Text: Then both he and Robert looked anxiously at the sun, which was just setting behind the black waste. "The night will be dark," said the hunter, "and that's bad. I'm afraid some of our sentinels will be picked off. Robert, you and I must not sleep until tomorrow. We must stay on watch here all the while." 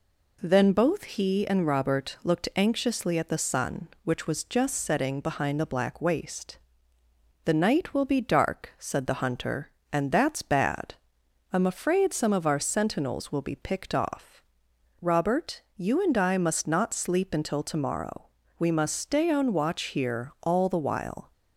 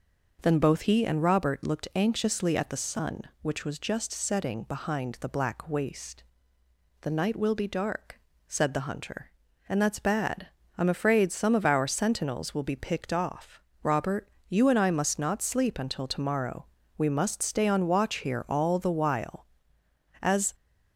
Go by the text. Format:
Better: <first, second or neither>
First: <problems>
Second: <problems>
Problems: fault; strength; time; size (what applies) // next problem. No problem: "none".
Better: first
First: none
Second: goes on to say "As"; slight; from 20.2 s on; 0.32 s long